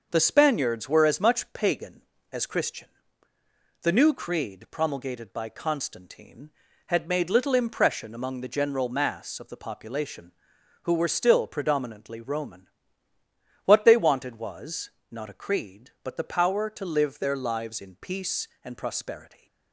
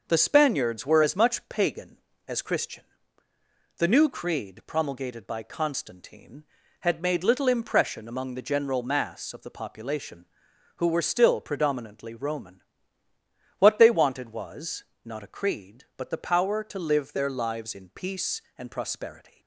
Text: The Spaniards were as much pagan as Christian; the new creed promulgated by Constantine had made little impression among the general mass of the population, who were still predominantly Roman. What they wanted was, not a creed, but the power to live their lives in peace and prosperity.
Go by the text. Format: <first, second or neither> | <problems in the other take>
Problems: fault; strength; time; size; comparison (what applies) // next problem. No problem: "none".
neither | starts louder than the rest; the same in both